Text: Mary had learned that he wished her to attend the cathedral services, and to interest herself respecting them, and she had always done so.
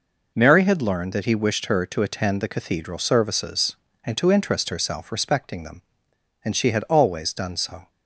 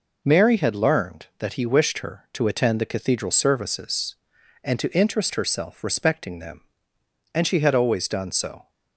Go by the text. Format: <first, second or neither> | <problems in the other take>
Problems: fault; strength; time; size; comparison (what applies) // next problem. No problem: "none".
neither | none